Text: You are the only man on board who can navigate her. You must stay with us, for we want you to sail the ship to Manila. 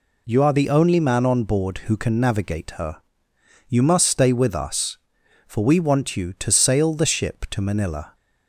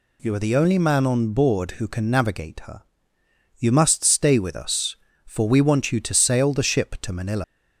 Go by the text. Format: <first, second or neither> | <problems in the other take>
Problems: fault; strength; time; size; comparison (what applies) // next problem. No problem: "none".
first | leaves "Manila" unfinished; at 7.4 s; 125 ms